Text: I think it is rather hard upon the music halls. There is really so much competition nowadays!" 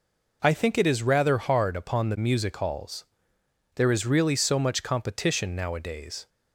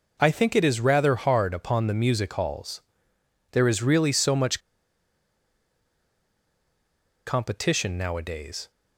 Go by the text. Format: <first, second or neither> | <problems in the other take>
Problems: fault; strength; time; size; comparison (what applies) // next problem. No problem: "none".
first | pauses between "much" and "competition"; strong; at 4.6 s; 2.6 s long